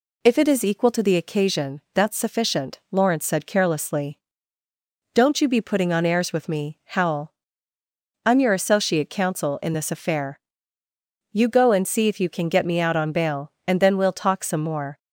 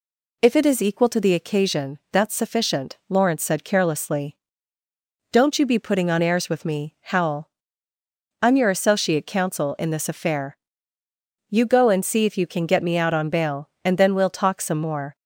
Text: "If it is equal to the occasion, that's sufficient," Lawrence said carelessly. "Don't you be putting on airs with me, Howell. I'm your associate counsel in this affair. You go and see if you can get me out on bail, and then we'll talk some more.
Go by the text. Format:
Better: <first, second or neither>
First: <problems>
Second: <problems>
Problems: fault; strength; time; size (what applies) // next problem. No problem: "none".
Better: neither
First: none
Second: none